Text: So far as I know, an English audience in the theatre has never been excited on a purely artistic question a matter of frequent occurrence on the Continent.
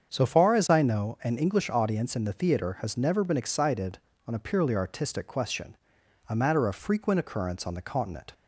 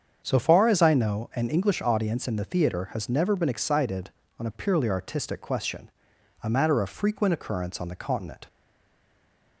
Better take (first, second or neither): first